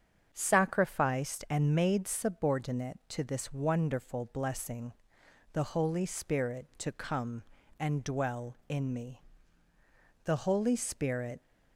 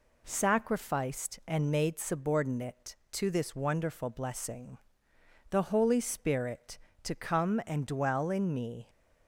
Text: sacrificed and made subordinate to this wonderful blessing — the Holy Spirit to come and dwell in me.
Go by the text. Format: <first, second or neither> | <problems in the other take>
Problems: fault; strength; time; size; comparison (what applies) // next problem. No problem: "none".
second | starts louder than the rest; strong; until 1.3 s; 7.5 dB // goes on to say "The Holy Spirit"; noticeable; from 10.2 s on; 1.1 s long